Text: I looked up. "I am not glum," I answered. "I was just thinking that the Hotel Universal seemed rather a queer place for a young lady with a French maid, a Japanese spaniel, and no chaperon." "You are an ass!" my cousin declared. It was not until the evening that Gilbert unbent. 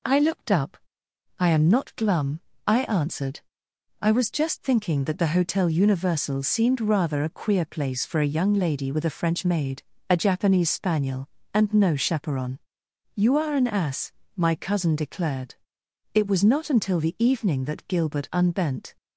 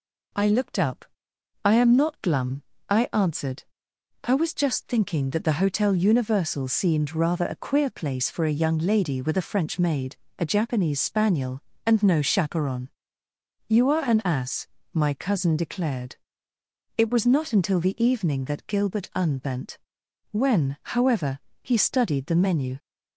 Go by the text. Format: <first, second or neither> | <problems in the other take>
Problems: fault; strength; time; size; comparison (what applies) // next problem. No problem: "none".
first | goes on to say "When however he studied the menu"; strong; from 20.3 s on; 2.4 s long